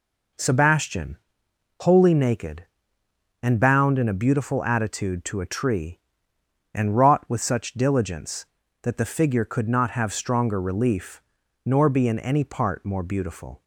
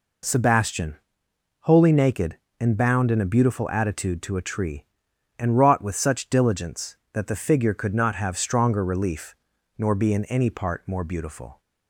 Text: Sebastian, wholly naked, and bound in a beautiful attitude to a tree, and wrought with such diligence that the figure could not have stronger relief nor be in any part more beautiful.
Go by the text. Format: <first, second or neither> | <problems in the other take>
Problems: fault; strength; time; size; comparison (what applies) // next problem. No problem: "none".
neither | pauses between "relief" and "nor"; the same in both